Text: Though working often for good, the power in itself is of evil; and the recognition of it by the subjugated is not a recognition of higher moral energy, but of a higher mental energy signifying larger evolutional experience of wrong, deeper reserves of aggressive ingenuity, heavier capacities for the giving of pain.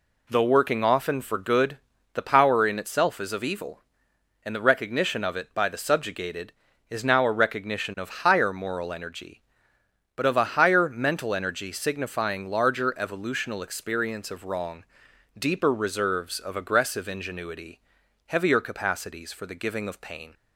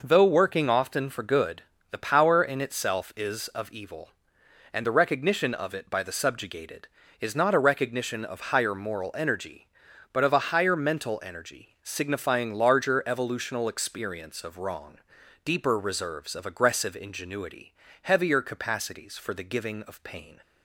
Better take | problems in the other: second | says "now" for "not"; at 7.0 s

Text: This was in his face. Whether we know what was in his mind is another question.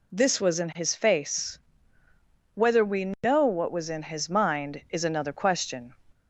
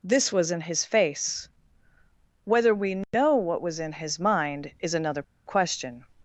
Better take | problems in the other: first | pauses between "another" and "question"; slight; at 5.2 s; 0.23 s long

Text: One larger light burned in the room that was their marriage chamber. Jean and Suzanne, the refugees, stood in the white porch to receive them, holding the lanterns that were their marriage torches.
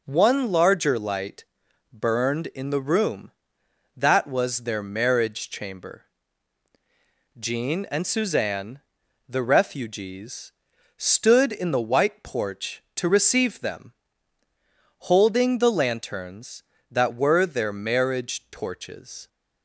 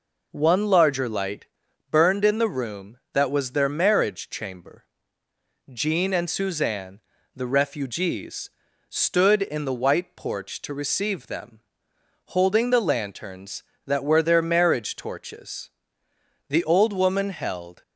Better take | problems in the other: first | pauses between "light" and "burned"; at 1.4 s; 0.44 s long; noticeable in the first // goes on to say "The old woman held"; from 16.4 s on; 1.3 s long

